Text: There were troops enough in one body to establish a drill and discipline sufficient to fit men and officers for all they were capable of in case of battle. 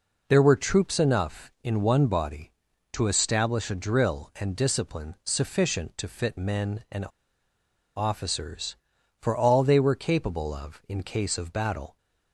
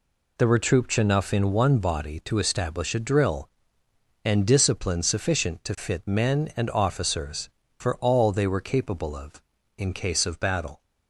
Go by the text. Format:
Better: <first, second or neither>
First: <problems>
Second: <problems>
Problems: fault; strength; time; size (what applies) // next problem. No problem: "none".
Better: second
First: pauses between "and" and "officers"; noticeable; at 7.0 s; 0.91 s long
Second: none